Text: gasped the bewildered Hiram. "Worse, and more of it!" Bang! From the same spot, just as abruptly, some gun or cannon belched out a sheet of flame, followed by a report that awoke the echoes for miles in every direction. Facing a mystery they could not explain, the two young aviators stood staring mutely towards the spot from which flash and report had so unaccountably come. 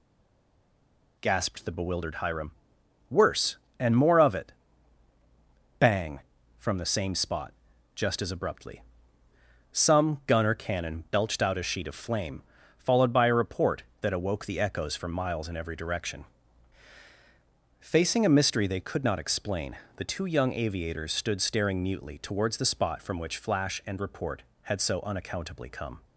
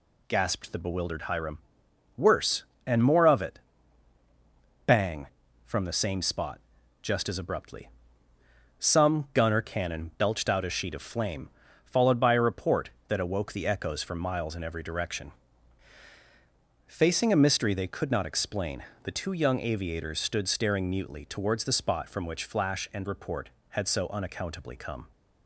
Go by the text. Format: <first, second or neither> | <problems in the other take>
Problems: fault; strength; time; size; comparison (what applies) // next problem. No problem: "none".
second | stays silent before the first word; noticeable; until 1.1 s; 1.1 s long